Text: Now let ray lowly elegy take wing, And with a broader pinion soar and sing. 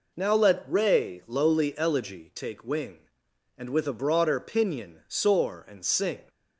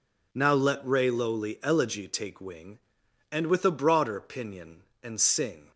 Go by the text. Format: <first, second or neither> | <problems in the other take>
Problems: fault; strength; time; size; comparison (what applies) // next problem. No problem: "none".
first | skips "soar"; at 4.9 s